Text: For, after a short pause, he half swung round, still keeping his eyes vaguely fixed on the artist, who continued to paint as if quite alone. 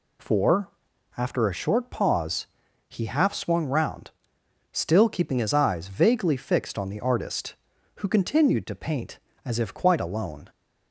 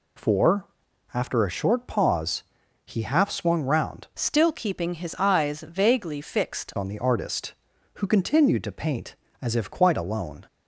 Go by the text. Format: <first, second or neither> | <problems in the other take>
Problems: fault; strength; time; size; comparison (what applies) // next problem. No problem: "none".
first | changes voice from "still" to "fixed"; from 4.1 to 6.7 s; 2.6 s long